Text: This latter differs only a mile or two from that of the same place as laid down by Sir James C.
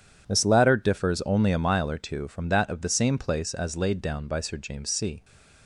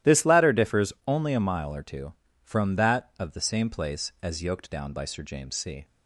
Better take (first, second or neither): first